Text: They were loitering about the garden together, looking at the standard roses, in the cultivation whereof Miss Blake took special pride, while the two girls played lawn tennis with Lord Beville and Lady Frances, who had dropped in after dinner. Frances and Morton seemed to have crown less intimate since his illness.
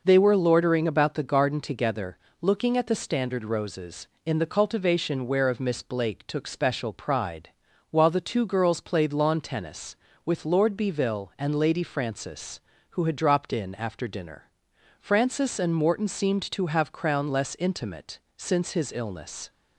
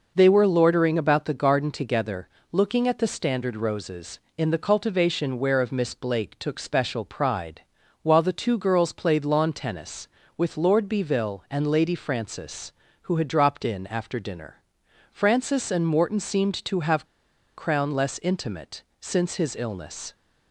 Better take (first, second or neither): first